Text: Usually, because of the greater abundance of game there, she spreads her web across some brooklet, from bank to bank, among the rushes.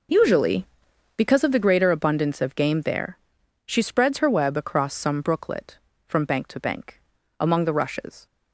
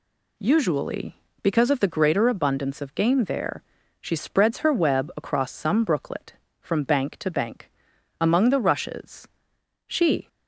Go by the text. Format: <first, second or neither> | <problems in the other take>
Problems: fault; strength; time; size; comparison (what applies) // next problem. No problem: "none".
first | goes on to say "She"; slight; from 9.8 s on; 0.40 s long